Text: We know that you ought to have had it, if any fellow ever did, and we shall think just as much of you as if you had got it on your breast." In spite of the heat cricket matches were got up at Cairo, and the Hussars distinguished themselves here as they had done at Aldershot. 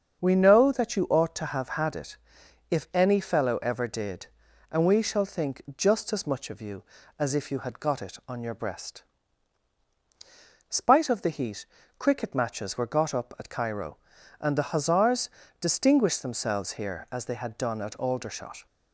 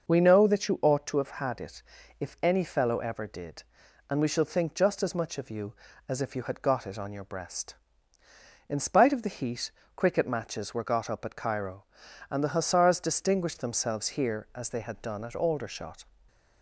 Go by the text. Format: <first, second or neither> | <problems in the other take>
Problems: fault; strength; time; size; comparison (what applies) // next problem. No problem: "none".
second | starts louder than the rest; until 1.2 s; 7 dB // pauses between "think" and "just"; slight; at 5.6 s; 0.16 s long // skips "In"; at 9.8 s // pauses between "heat" and "cricket"; slight; at 11.6 s; 0.32 s long; slight in the second // pauses between "Hussars" and "distinguished"; slight; at 15.2 s; 0.32 s long